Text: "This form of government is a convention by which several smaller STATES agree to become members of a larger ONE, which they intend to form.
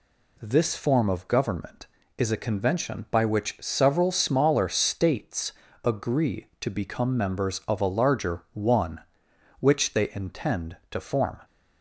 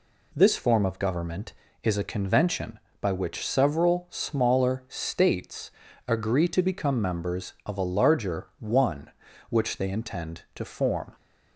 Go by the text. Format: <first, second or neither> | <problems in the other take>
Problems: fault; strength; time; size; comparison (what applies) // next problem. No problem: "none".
neither | pauses between "STATES" and "agree"; the same in both